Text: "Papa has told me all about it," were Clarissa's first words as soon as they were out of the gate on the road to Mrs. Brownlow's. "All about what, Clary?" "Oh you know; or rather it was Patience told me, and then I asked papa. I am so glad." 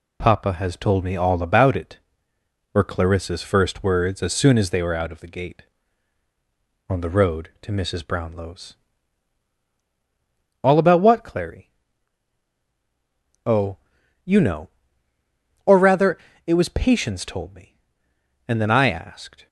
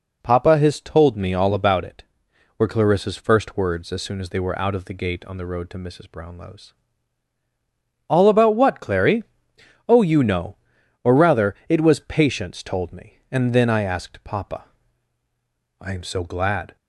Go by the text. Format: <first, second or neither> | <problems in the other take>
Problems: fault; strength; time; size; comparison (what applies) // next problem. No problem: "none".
second | pauses between "Oh" and "you"; at 13.7 s; 0.44 s long // pauses between "rather" and "it"; slight; at 16.1 s; 0.26 s long // stops before "papa I am so glad"; at 19.4 s